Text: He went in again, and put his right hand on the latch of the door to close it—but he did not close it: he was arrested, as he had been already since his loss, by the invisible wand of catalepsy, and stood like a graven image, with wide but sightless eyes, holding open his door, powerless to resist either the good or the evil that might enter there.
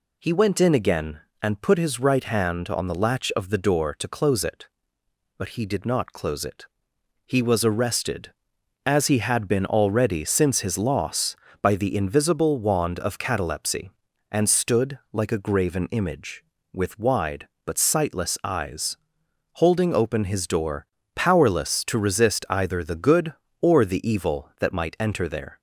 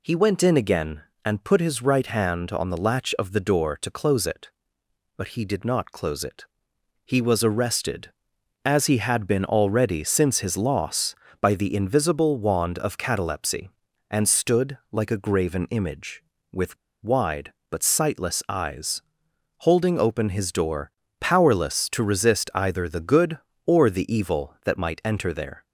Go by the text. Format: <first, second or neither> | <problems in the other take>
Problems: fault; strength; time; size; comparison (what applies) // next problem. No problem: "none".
first | pauses between "with" and "wide"; slight; at 16.7 s; 0.28 s long